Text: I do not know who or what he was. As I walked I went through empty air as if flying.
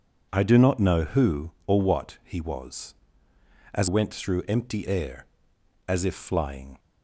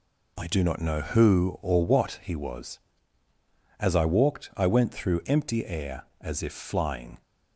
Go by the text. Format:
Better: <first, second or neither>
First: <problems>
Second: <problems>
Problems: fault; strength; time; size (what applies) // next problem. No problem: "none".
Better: second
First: skips "I walked I"; at 3.8 s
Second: none